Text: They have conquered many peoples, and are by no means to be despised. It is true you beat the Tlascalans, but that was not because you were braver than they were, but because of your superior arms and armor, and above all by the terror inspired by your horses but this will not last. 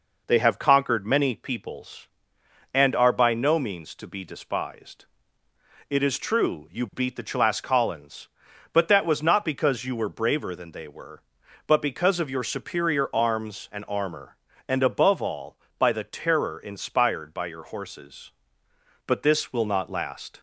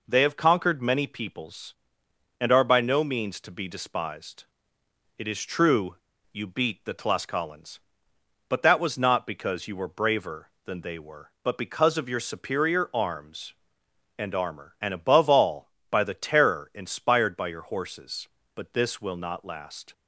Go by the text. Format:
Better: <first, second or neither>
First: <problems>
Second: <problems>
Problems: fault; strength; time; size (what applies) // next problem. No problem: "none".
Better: first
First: none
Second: pauses between "true" and "you"; at 5.9 s; 0.37 s long